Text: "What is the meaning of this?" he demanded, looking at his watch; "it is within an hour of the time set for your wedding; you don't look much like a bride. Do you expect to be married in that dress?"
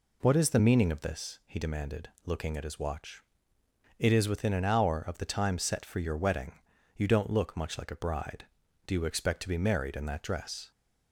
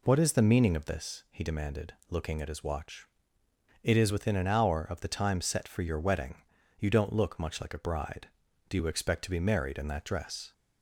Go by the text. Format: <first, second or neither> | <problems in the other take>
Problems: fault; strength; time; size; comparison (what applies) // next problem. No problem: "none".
neither | none